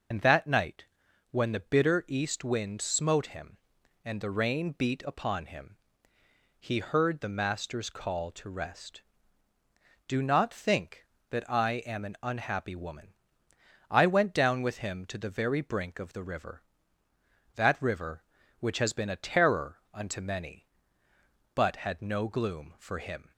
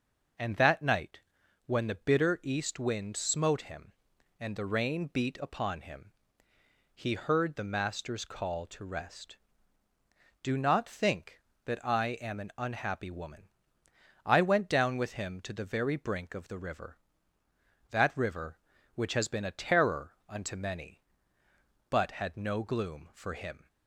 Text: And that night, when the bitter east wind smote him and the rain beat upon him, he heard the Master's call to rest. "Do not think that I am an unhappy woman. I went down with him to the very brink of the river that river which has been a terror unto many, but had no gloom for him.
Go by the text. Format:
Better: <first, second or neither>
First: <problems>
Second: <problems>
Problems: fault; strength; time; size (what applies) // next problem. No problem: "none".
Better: second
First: loses the start of "And"; at 0.1 s; 65 ms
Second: none